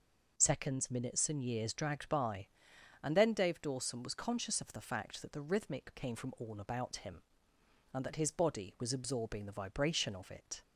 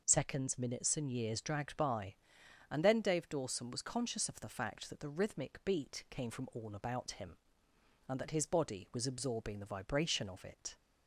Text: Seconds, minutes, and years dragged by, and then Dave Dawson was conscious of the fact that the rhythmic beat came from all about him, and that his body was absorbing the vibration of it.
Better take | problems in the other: second | skips "beat"; at 5.9 s

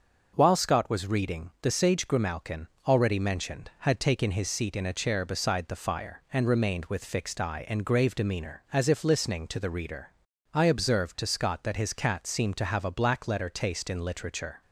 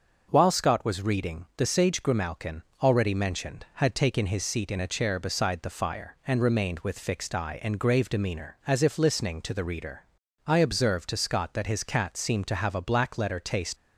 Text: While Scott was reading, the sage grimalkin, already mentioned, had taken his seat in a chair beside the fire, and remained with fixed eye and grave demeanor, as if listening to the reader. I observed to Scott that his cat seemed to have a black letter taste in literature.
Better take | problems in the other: first | starts louder than the rest; until 1.3 s; 6 dB; also in the first // stops before "in literature"; at 13.7 s

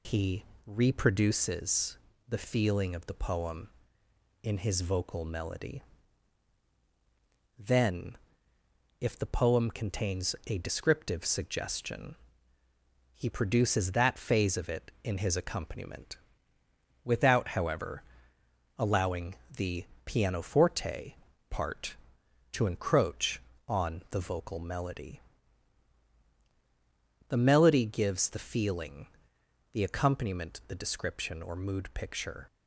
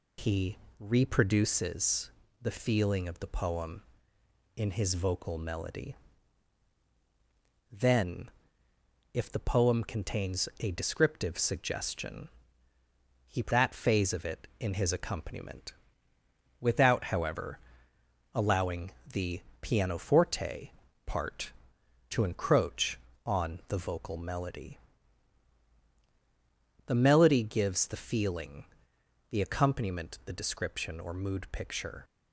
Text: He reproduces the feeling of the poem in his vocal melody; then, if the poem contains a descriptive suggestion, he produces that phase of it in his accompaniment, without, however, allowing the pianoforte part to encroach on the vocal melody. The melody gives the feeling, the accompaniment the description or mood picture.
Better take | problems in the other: first | pauses between "He" and "reproduces"; slight; at 0.5 s; 0.24 s long; slight in the first // pauses between "reproduces" and "the"; slight; at 2.1 s; 0.30 s long; slight in the first // skips "produces"; at 13.5 s // pauses between "allowing" and "the"; slight; at 18.9 s; 0.22 s long; slight in the first // pauses between "the" and "pianoforte"; slight; at 19.4 s; 0.18 s long; slight in the first // pauses between "pianoforte" and "part"; slight; at 20.7 s; 0.34 s long; slight in the first

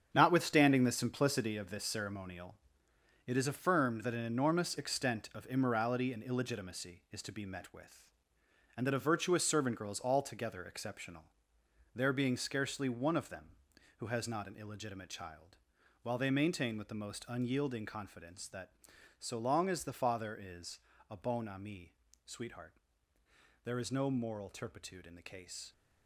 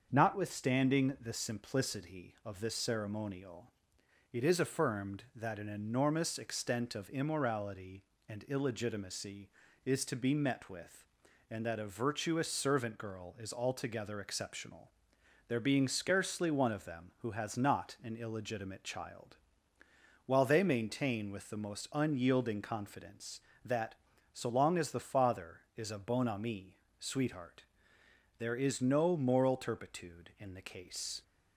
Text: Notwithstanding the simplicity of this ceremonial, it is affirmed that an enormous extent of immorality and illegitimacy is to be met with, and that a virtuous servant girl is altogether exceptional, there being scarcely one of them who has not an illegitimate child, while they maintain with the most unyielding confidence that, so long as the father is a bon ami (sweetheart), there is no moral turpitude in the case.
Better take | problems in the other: second | gets quieter; strong; throughout; 10 dB // starts louder than the rest; strong; until 1.1 s; 8 dB; also in the second // pauses between "is" and "a"; slight; at 20.8 s; 0.28 s long

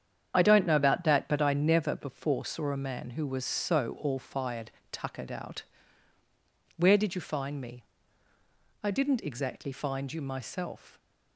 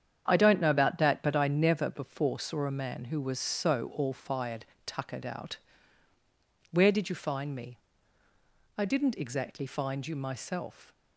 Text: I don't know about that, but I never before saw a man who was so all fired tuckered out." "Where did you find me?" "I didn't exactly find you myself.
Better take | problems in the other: second | loses the start of "I"; at 0.3 s; 35 ms // starts louder than the rest; strong; until 1.3 s; 8.5 dB; strong in the second // pauses between "fired" and "tuckered"; slight; at 4.7 s; 0.20 s long; slight in the second

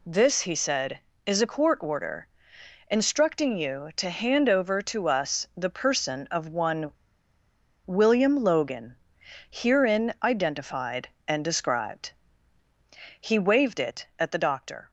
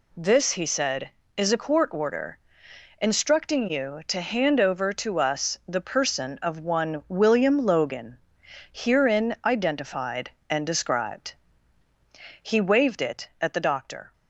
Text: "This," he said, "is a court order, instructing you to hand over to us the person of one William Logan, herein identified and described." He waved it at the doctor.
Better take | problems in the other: second | pauses between "one" and "William"; noticeable; at 6.9 s; 0.95 s long

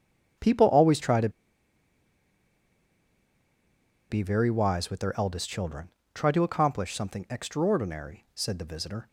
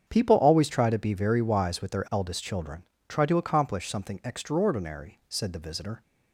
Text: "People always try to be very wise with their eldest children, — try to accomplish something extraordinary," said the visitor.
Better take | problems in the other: second | starts louder than the rest; strong; until 4.2 s; 8 dB; strong in the second // pauses between "to" and "be"; strong; at 1.2 s; 2.8 s long

